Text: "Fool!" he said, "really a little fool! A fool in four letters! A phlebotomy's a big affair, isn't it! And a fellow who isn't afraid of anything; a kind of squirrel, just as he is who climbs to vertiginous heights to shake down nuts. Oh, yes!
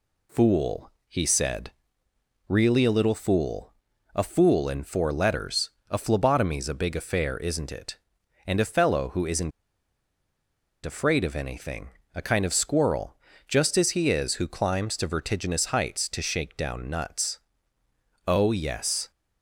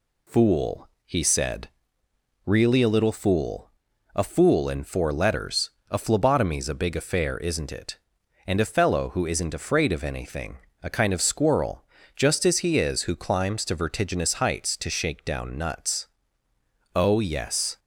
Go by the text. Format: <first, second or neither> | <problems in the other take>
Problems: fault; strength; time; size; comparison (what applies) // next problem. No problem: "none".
second | pauses between "isn't" and "afraid"; strong; at 9.5 s; 1.3 s long